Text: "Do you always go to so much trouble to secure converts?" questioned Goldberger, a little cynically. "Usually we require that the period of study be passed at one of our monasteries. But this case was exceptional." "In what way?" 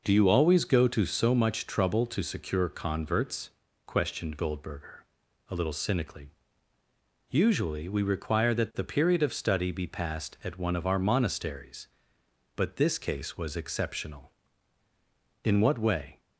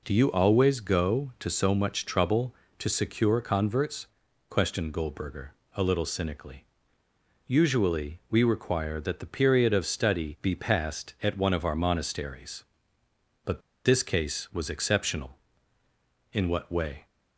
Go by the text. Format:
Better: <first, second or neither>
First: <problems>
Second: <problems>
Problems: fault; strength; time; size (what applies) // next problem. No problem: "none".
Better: first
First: none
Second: pauses between "But" and "this"; slight; at 13.6 s; 0.24 s long